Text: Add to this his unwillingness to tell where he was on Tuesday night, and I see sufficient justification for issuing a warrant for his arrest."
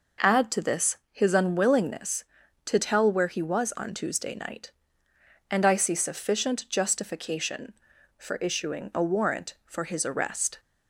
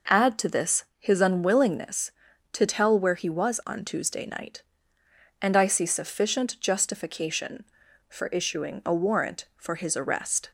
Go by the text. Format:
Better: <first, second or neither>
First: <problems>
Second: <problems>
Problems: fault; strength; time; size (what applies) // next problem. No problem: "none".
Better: neither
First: pauses between "this" and "his"; slight; at 0.9 s; 0.16 s long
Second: pauses between "this" and "his"; slight; at 0.8 s; 0.16 s long